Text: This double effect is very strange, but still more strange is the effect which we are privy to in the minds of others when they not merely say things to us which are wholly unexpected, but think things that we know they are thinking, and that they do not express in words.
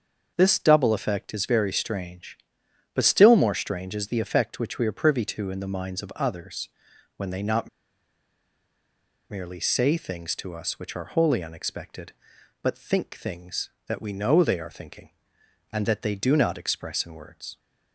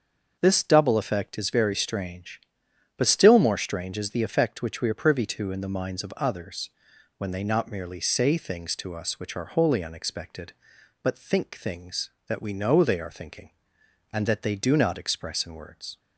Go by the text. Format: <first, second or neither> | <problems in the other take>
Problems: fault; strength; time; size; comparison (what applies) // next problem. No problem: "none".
second | starts louder than the rest; until 1.3 s; 6.5 dB; also in the second // pauses between "others" and "when"; noticeable; at 6.6 s; 0.48 s long; noticeable in the second // pauses between "not" and "merely"; strong; at 7.6 s; 1.6 s long